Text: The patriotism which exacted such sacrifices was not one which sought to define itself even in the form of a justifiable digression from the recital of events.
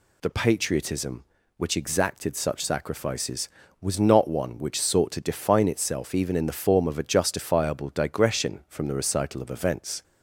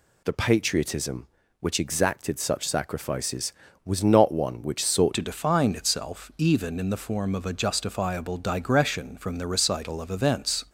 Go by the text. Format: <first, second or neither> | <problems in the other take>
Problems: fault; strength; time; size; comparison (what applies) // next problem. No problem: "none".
first | changes voice at "to"; from 5.1 s on; 5.5 s long